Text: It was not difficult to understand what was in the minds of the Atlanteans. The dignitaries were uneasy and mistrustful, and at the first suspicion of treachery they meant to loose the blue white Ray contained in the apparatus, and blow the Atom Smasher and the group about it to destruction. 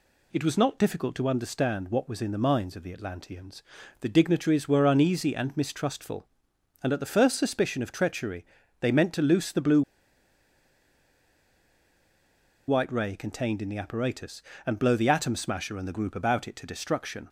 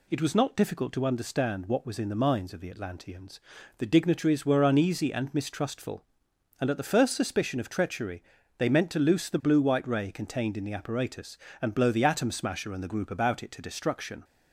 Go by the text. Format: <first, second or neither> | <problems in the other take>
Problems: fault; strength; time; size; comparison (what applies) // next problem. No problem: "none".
second | pauses between "treachery" and "they"; slight; at 8.4 s; 0.34 s long; slight in the second // pauses between "blue" and "white"; strong; at 9.8 s; 2.8 s long